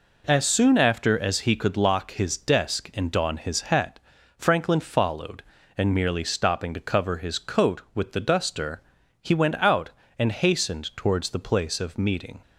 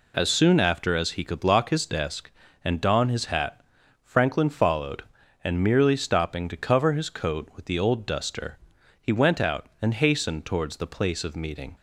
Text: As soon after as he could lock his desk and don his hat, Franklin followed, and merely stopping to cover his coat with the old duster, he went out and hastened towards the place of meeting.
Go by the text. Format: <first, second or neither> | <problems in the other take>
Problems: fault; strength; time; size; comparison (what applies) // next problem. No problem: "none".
second | skips "old"; at 8.1 s